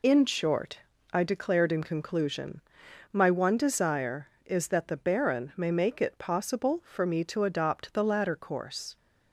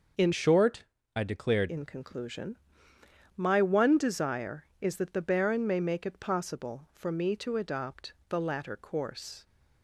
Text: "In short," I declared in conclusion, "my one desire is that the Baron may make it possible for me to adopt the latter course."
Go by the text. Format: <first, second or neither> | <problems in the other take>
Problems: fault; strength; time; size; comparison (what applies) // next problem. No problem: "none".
first | starts louder than the rest; noticeable; until 1.4 s; 6 dB // changes voice from "short" to "declared"; from 0.3 to 1.6 s; 1.3 s long // pauses between "adopt" and "the"; slight; at 8.1 s; 0.16 s long